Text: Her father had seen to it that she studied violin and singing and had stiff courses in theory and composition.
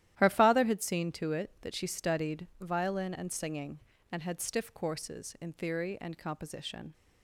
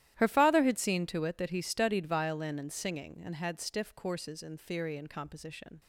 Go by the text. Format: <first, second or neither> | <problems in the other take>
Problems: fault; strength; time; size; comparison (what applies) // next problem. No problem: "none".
first | starts louder than the rest; strong; until 1.2 s; 13 dB; strong in the first // says "he" for "she"; at 1.4 s